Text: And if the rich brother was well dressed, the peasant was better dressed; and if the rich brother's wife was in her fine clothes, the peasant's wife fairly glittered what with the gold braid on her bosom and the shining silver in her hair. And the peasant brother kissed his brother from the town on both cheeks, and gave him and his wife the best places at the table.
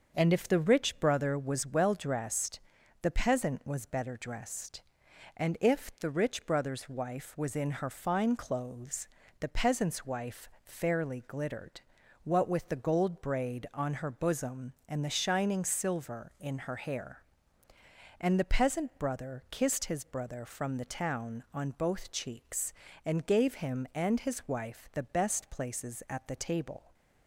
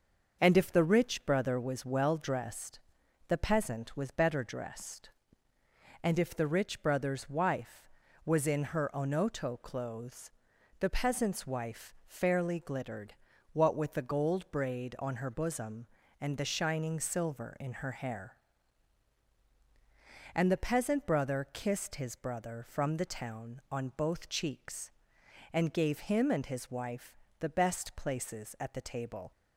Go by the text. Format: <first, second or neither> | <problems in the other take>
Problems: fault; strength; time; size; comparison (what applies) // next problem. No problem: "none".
first | starts louder than the rest; until 1.4 s; 6.5 dB; also in the first // says "onoto" for "fine"; at 8.9 s // pauses between "glittered" and "what"; at 13.1 s; 0.38 s long; also in the first // pauses between "wife" and "the"; slight; at 27.1 s; 0.22 s long